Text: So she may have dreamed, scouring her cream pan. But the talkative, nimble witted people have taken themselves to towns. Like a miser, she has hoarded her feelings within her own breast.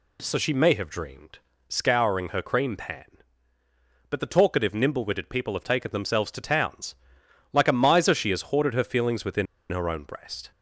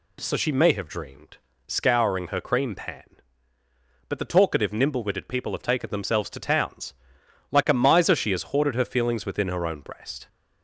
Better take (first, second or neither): second